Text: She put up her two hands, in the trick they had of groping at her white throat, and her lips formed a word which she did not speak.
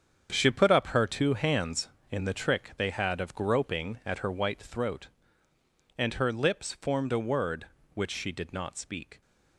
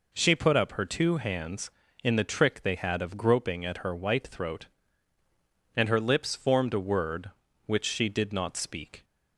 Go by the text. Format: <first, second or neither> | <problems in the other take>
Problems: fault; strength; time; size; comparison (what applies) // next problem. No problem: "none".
second | gets quieter; strong; throughout; 10.5 dB